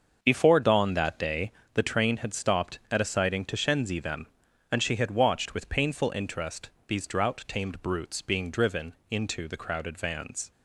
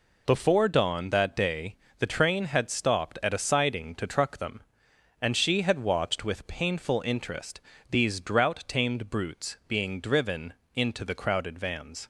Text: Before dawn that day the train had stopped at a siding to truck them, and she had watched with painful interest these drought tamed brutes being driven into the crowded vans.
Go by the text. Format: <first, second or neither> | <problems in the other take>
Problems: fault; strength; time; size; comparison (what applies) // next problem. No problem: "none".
second | starts louder than the rest; until 1.2 s; 6.5 dB // pauses between "day" and "the"; slight; at 1.5 s; 0.22 s long; slight in the second // says "shenzi" for "truck"; at 3.5 s // pauses between "interest" and "these"; slight; at 6.6 s; 0.20 s long; slight in the second // pauses between "driven" and "into"; slight; at 8.9 s; 0.16 s long; slight in the second